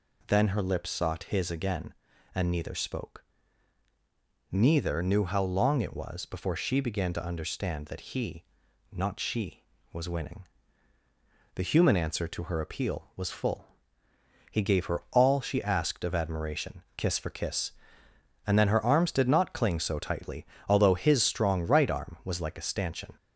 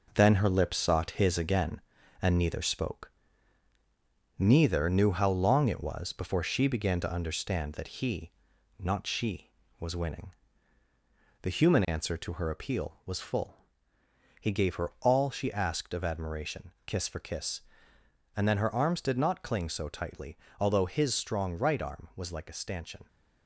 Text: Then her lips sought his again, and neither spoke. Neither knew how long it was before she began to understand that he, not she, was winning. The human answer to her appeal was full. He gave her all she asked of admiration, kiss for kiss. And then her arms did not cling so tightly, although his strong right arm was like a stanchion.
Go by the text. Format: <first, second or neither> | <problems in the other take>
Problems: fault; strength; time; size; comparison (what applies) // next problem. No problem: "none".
first | gets quieter; noticeable; throughout; 6 dB